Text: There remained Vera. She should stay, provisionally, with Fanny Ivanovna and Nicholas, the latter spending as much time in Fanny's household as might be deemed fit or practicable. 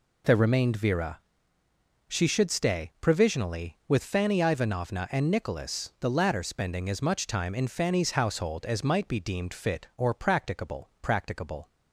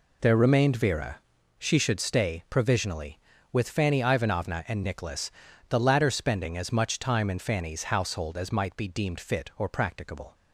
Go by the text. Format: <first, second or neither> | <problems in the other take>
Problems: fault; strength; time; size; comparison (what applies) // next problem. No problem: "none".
second | says "practicable" twice; at 11.0 s